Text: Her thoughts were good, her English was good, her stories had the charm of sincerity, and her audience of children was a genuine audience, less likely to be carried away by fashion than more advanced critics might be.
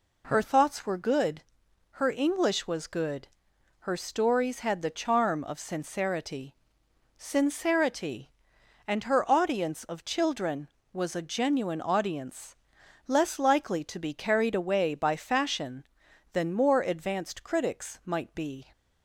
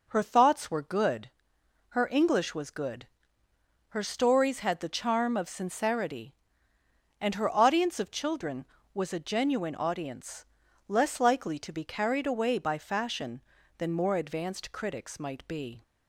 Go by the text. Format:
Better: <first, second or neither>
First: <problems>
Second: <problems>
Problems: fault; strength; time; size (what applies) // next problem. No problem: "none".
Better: second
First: says "sincerity" twice; at 7.1 s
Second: none